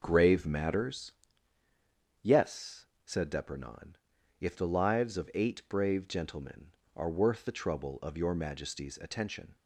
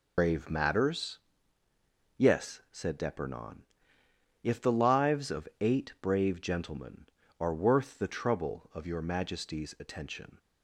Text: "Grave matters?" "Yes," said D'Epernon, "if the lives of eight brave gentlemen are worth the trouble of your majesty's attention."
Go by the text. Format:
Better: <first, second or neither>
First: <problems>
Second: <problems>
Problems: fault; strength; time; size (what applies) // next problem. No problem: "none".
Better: first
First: none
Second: loses the start of "Grave"; at 0.1 s; 100 ms